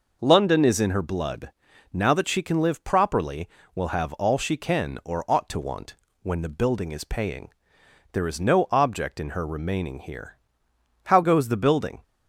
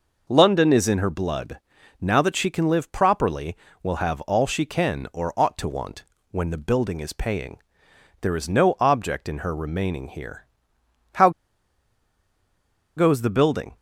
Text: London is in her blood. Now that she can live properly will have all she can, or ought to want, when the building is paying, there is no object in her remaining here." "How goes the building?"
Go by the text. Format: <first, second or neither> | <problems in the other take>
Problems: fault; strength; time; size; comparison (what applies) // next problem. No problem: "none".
first | pauses between "How" and "goes"; strong; at 11.2 s; 1.6 s long